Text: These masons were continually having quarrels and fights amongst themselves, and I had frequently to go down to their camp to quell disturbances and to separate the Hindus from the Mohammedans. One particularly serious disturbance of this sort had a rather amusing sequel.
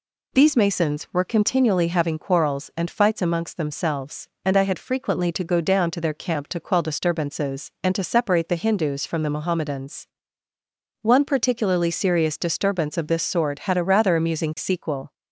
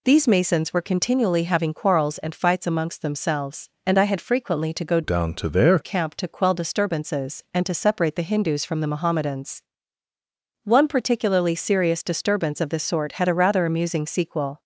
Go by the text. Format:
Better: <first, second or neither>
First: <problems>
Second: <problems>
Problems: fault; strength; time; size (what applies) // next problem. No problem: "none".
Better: first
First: none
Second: changes voice from "down" to "their"; from 5.0 to 5.7 s; 0.7 s long